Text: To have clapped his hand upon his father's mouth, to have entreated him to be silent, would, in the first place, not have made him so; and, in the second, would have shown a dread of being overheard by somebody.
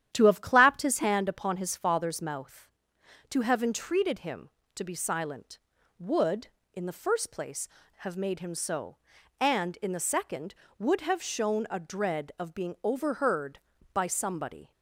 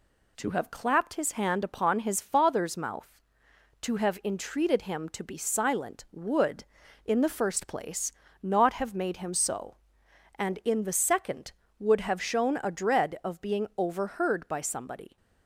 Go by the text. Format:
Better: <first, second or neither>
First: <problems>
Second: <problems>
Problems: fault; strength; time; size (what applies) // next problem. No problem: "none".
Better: second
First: starts louder than the rest; strong; until 1.1 s; 10.5 dB // skips "not"; at 7.8 s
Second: none